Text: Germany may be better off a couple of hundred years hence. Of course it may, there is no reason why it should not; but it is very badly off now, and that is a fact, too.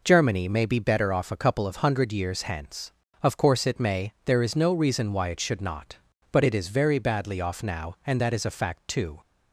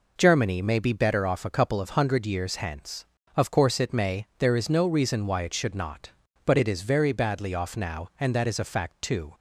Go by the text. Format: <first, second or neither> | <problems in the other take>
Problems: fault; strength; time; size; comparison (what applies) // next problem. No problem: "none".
neither | none